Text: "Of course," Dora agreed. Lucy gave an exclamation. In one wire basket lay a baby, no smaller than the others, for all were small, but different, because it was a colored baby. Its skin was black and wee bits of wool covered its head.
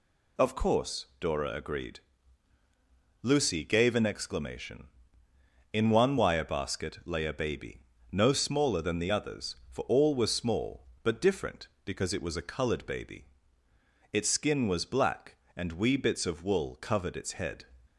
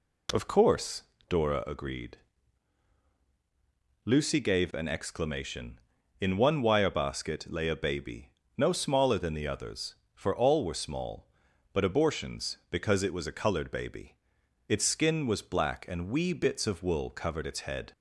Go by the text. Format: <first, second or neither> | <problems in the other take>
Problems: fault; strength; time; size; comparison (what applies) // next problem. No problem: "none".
first | says "abortions" for "different"; at 11.8 s